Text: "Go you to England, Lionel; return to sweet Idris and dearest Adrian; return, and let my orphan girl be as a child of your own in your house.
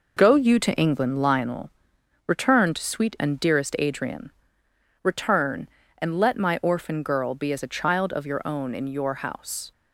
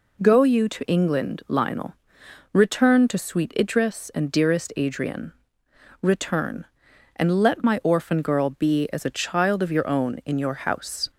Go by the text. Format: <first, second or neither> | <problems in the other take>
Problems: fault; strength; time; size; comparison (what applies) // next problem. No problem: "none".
second | skips "Idris"; at 3.1 s